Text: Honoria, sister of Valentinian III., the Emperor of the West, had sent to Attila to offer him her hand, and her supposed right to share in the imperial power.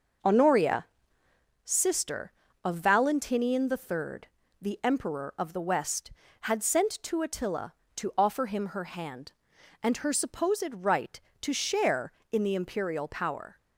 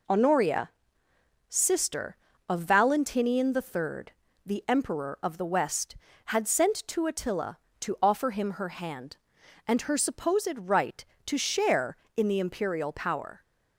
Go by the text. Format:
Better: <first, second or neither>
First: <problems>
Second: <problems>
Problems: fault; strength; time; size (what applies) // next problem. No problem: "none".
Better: second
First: starts louder than the rest; noticeable; until 1.5 s; 6 dB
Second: none